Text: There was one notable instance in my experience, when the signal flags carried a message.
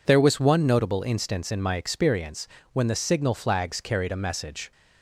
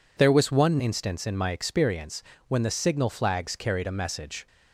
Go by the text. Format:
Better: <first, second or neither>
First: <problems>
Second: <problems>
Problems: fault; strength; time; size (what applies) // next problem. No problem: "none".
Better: first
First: none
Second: skips "notable"; at 0.7 s